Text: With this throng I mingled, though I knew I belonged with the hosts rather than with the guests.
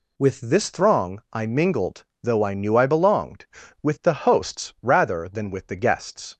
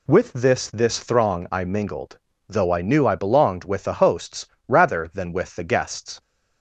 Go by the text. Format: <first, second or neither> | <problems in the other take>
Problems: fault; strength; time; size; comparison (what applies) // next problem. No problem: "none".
first | says "this" twice; at 0.6 s // pauses between "hosts" and "rather"; slight; at 4.4 s; 0.22 s long